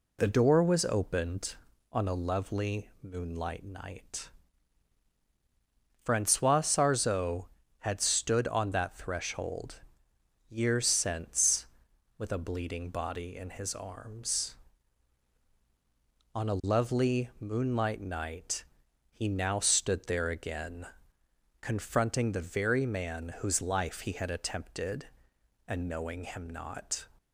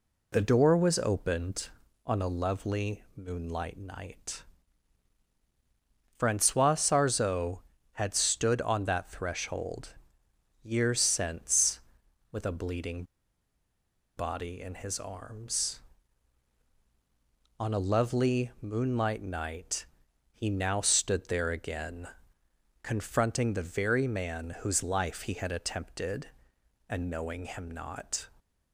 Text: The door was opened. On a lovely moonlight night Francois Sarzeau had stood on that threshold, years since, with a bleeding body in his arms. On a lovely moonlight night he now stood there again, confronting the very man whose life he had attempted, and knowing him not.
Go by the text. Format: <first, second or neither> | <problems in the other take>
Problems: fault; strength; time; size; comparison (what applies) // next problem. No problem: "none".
first | pauses between "night" and "Francois"; strong; at 4.4 s; 1.7 s long; strong in the first // pauses between "bleeding" and "body"; at 13.0 s; 1.1 s long // pauses between "night" and "he"; noticeable; at 19.8 s; 0.48 s long; noticeable in the first